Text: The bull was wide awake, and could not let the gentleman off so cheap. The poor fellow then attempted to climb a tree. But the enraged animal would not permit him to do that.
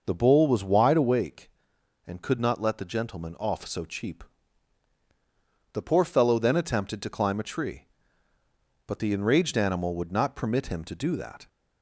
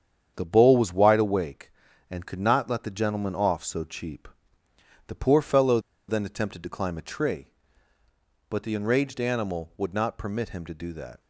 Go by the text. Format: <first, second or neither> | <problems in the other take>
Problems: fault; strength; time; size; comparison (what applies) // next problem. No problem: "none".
first | starts louder than the rest; strong; until 1.3 s; 8 dB // pauses between "fellow" and "then"; slight; at 5.7 s; 0.29 s long